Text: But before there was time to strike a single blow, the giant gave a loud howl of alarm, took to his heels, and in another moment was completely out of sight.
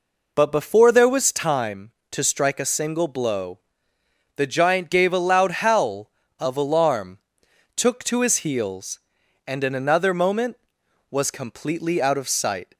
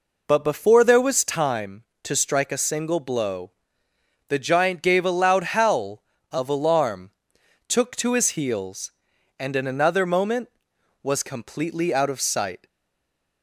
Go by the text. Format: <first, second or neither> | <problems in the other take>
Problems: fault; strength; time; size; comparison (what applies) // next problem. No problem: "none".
first | stays silent after the last word; slight; from 12.6 s on; 0.8 s long